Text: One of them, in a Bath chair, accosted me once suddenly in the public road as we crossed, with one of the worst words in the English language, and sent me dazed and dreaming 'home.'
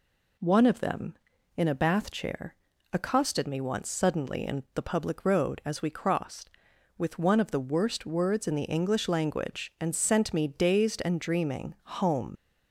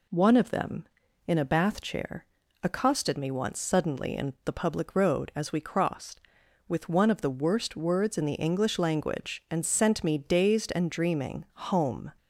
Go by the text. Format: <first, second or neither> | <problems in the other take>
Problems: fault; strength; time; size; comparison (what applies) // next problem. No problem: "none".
second | leaves "home" unfinished; at 12.3 s; 110 ms